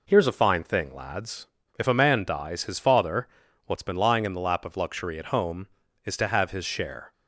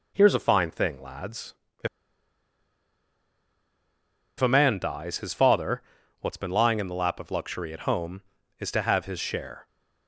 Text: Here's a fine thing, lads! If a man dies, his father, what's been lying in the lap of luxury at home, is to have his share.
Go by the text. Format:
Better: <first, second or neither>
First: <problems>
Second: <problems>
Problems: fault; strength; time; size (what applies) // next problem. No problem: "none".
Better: first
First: none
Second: pauses between "If" and "a"; strong; at 1.8 s; 2.5 s long